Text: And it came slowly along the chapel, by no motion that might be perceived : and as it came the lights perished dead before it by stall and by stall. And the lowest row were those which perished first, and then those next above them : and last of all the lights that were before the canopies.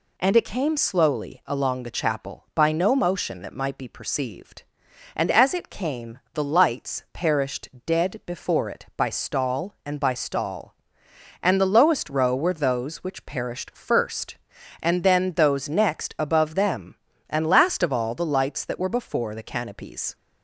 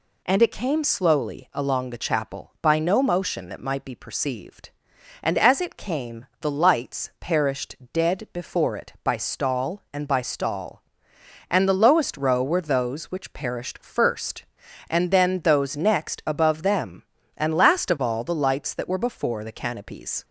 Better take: neither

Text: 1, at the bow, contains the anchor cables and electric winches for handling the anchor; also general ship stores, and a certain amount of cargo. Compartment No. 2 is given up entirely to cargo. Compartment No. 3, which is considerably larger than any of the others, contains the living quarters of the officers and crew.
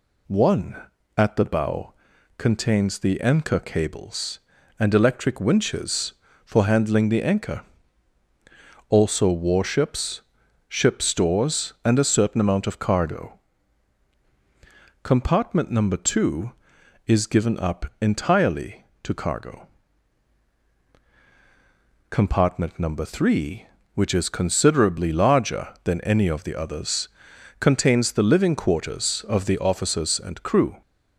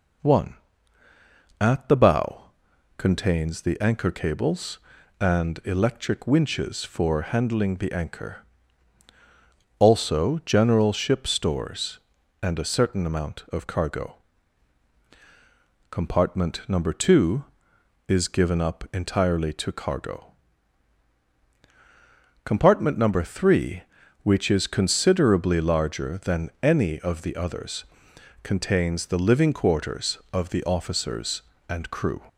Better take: second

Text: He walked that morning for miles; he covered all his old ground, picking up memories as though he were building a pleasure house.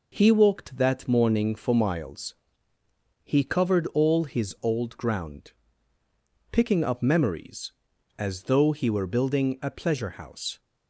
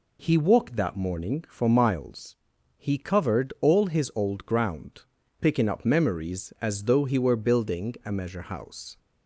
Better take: first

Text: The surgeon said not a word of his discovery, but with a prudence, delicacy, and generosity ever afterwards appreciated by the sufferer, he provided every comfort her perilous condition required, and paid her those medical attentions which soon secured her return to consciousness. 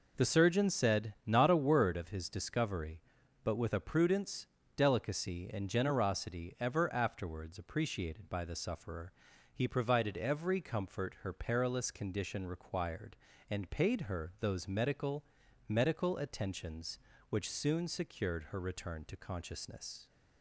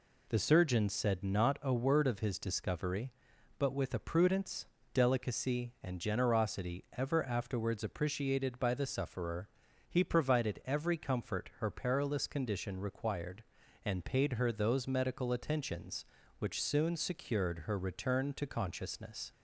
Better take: second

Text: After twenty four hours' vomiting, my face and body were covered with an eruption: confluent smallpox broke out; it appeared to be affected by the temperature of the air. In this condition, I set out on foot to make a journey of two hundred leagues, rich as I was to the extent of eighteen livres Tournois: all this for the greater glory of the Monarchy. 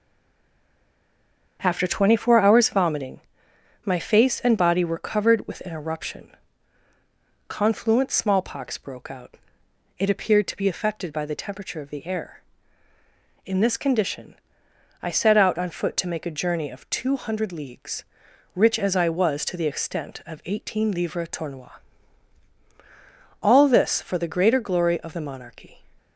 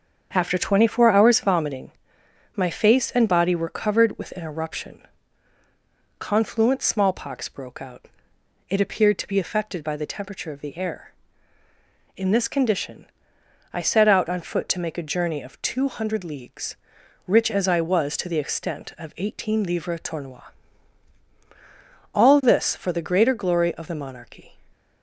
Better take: second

